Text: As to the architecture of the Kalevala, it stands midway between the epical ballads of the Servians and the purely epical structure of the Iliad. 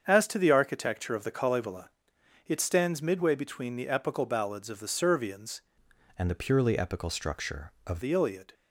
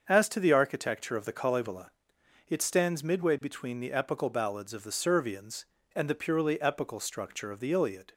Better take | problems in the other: second | starts louder than the rest; strong; until 1.0 s; 7.5 dB; also in the second // changes voice from "and" to "of"; from 6.1 to 7.9 s; 1.8 s long

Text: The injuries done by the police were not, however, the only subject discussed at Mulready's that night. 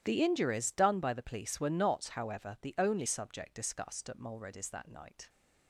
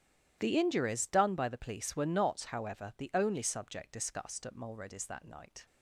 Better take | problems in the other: neither | starts louder than the rest; strong; the same in both

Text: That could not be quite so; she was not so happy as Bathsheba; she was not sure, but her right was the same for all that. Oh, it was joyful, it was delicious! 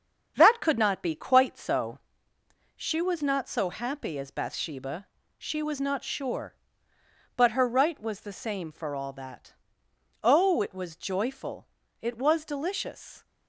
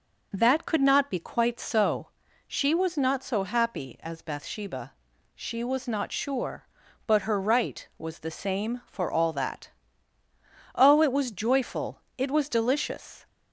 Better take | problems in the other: second | gets quieter; throughout; 6.5 dB

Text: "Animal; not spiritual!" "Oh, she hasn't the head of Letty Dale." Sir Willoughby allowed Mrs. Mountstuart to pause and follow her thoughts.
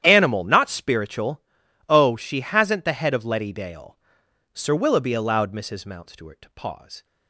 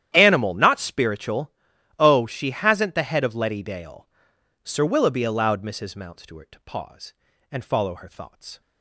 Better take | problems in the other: second | starts louder than the rest; strong; until 1.0 s; 10.5 dB; strong in the second // stops before "and follow her thoughts"; at 7.0 s

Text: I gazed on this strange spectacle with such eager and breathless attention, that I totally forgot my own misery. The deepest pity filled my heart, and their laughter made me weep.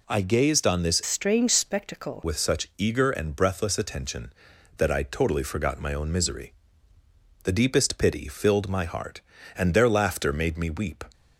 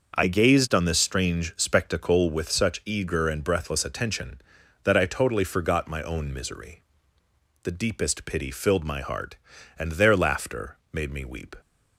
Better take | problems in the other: second | changes voice from "strange" to "spectacle"; from 1.0 to 2.2 s; 1.2 s long

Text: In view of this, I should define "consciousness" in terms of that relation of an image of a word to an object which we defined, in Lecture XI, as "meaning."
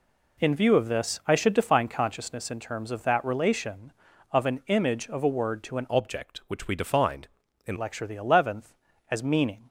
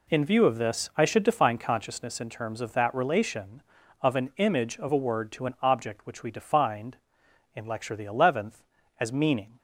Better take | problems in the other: second | changes voice from "object" to "in"; from 5.8 to 7.7 s; 1.9 s long

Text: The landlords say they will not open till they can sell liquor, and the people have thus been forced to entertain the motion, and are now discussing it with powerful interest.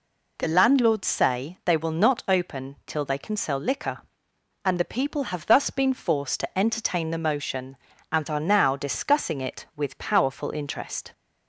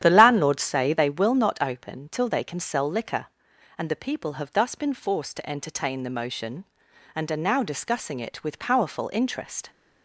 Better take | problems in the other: first | starts louder than the rest; strong; until 1.2 s; 10.5 dB

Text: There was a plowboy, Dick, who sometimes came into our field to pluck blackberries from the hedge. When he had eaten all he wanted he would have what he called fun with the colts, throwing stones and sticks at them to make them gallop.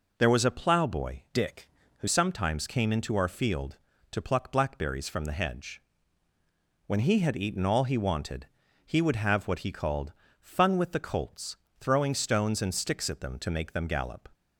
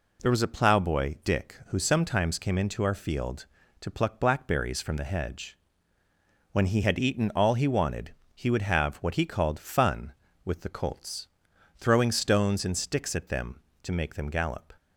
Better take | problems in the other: second | changes voice from "Dick" to "who"; from 1.3 to 2.0 s; 0.7 s long // pauses between "wanted" and "he"; at 8.4 s; 0.40 s long; slight in the second // pauses between "called" and "fun"; slight; at 10.1 s; 0.28 s long

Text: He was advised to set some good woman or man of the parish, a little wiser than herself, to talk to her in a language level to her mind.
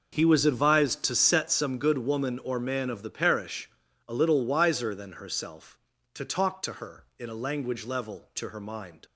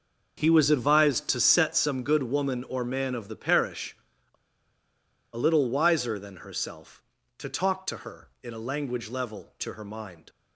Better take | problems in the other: first | pauses between "a" and "little"; at 4.3 s; 1.0 s long

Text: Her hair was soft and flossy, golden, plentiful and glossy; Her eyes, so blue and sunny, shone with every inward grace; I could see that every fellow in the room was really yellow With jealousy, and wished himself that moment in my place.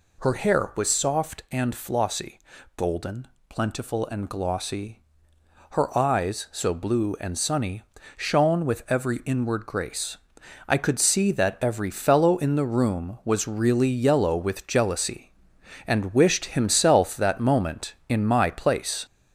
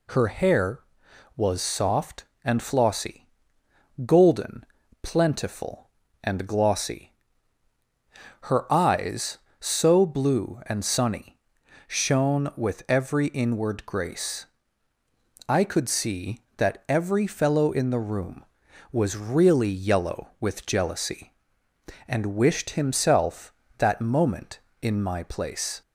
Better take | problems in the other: second | gets louder; noticeable; throughout; 4 dB

